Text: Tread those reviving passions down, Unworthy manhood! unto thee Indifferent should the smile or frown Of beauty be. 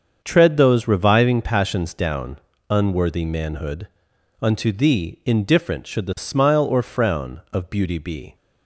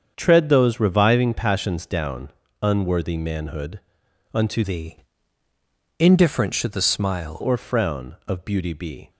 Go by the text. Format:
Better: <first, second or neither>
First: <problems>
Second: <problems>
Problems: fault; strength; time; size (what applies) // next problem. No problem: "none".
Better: first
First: starts louder than the rest; until 1.2 s; 7 dB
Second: starts louder than the rest; strong; until 1.1 s; 7.5 dB // changes voice from "thee" to "smile"; from 4.6 to 7.3 s; 2.7 s long // pauses between "thee" and "Indifferent"; at 4.9 s; 1.0 s long